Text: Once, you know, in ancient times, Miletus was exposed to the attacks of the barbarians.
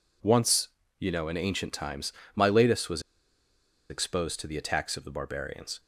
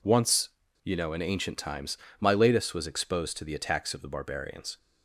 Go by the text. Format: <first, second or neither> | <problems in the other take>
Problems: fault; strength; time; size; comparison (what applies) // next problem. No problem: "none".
second | pauses between "was" and "exposed"; noticeable; at 3.0 s; 0.89 s long